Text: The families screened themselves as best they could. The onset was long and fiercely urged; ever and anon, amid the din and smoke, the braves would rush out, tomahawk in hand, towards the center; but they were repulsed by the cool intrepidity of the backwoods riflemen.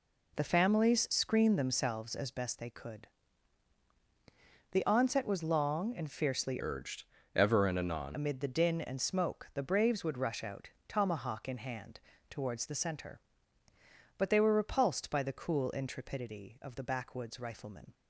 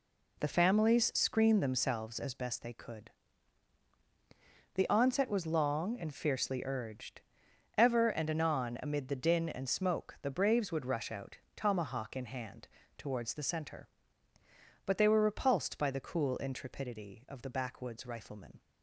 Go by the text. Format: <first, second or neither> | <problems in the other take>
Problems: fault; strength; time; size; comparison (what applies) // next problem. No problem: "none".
second | changes voice from "urged" to "anon"; from 6.5 to 8.1 s; 1.6 s long